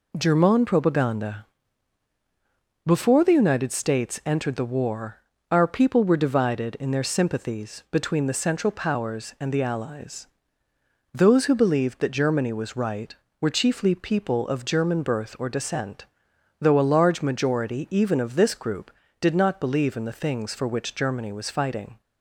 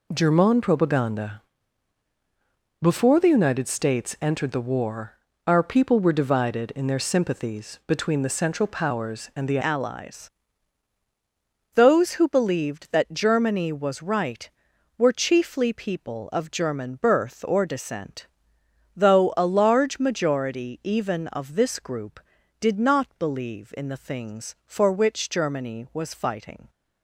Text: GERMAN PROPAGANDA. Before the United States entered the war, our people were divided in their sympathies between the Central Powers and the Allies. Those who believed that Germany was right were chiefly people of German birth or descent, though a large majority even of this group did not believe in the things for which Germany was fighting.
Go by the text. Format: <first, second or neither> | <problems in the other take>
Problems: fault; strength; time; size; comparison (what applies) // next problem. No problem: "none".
first | changes voice at "Allies"; from 9.6 s on; 17.0 s long